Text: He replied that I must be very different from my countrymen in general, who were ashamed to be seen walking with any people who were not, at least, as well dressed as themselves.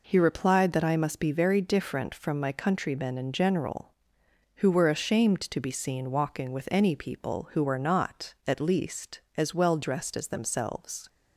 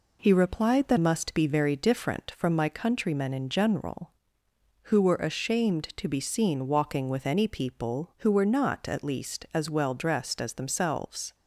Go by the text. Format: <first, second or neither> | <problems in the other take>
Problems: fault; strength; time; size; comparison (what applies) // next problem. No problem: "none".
first | skips "I"; at 0.9 s